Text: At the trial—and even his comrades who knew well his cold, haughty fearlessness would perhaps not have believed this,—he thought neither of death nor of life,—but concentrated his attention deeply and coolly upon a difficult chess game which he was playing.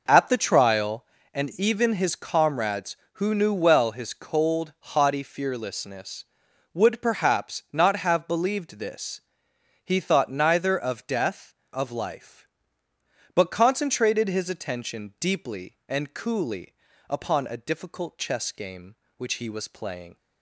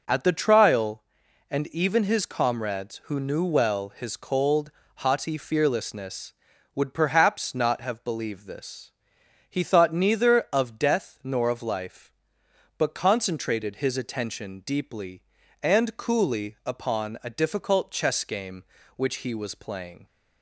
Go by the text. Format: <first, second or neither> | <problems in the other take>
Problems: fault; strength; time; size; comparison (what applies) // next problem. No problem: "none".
second | skips "nor"; at 11.6 s // pauses between "coolly" and "upon"; slight; at 16.7 s; 0.36 s long